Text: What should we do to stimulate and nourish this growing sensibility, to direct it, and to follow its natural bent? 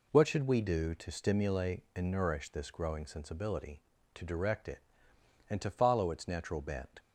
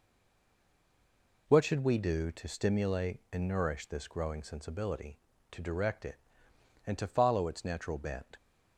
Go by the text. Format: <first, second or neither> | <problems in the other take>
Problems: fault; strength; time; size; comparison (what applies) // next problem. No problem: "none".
first | stays silent before the first word; noticeable; until 1.4 s; 1.4 s long